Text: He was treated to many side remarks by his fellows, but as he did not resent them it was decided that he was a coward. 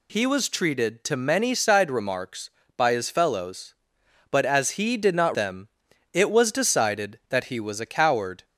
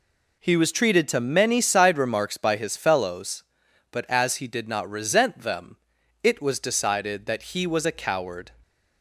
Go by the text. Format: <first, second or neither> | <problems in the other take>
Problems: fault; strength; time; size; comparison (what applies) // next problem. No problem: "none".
second | skips "resent"; at 5.3 s // pauses between "them" and "it"; noticeable; at 5.6 s; 0.46 s long; noticeable in the second